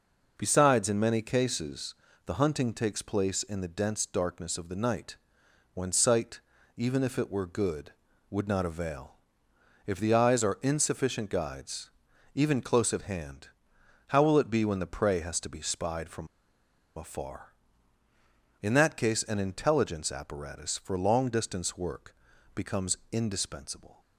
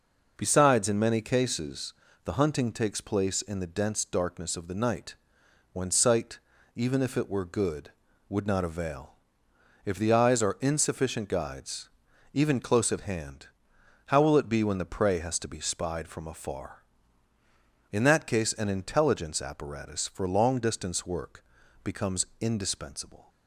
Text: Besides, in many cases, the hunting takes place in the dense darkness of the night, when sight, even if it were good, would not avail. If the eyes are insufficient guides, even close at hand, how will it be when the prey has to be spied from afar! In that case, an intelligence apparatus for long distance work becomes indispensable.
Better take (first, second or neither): second